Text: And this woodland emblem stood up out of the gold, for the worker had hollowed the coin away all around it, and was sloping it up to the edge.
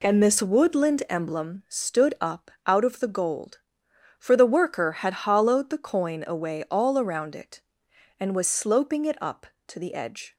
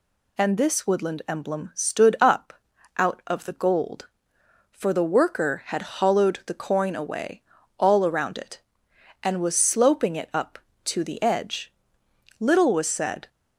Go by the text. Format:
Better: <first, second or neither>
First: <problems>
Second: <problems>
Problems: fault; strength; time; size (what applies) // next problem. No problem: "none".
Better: first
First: pauses between "up" and "out"; slight; at 2.5 s; 0.16 s long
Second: pauses between "up" and "out"; at 2.5 s; 0.44 s long // pauses between "away" and "all"; slight; at 7.4 s; 0.36 s long // goes on to say "Little was said"; noticeable; from 12.3 s on; 0.88 s long